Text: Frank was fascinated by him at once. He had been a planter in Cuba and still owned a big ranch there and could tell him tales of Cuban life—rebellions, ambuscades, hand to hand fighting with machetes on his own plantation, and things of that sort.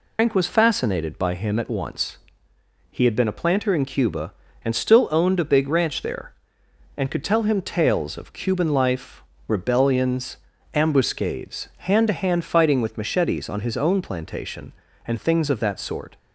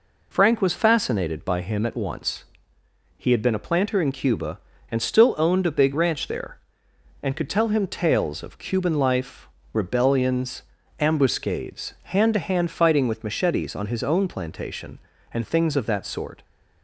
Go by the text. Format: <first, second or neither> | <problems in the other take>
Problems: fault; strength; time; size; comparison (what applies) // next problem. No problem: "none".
second | loses the start of "Frank"; at 0.1 s; 140 ms